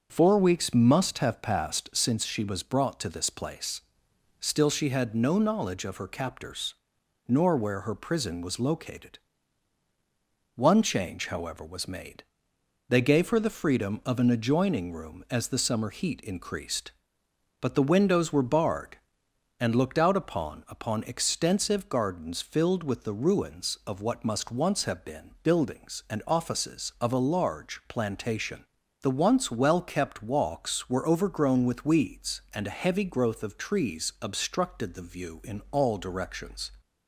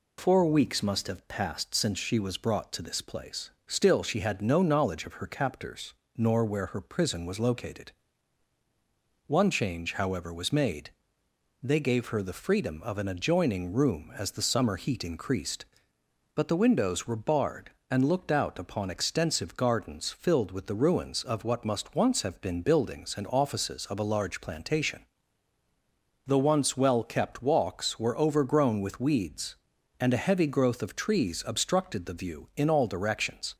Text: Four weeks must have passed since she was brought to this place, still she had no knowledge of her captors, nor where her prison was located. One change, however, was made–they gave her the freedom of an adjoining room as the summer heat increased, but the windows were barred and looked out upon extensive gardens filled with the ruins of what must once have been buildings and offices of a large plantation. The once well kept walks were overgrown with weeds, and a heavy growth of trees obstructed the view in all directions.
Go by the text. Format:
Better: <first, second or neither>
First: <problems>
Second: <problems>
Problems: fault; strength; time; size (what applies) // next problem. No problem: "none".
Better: second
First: says "upon" twice; at 20.6 s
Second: none